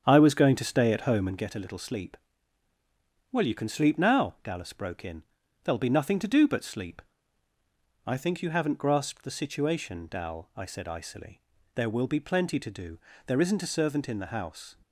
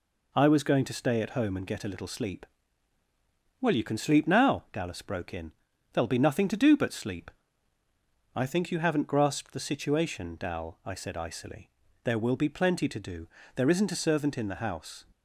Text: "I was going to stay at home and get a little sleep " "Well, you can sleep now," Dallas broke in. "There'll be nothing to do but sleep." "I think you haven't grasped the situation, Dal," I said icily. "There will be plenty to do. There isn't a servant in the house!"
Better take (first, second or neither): second